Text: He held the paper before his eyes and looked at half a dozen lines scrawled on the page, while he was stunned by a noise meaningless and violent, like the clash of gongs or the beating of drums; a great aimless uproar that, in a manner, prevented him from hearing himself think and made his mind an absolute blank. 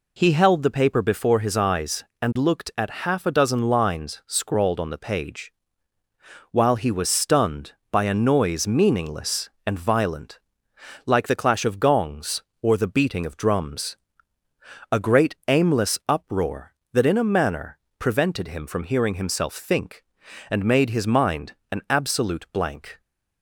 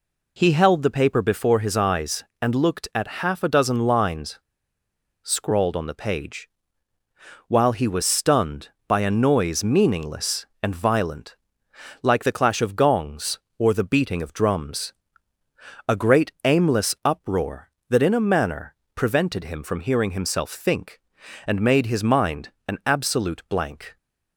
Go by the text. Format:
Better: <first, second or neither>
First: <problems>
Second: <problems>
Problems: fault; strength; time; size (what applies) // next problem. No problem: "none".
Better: first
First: pauses between "mind" and "an"; slight; at 21.5 s; 0.18 s long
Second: pauses between "lines" and "scrawled"; noticeable; at 4.3 s; 0.85 s long // pauses between "mind" and "an"; slight; at 22.5 s; 0.18 s long